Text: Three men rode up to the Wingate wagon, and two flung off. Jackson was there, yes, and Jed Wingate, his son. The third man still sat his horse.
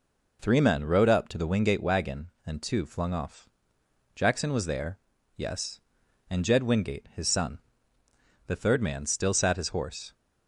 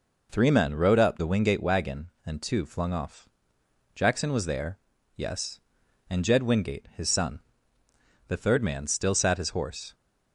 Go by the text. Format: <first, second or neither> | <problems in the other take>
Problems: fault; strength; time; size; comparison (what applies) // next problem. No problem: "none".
first | skips "to"; at 1.1 s